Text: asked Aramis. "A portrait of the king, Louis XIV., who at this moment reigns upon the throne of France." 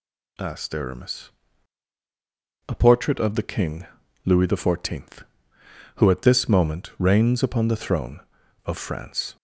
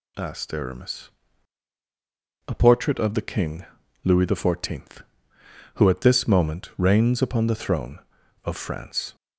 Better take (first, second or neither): neither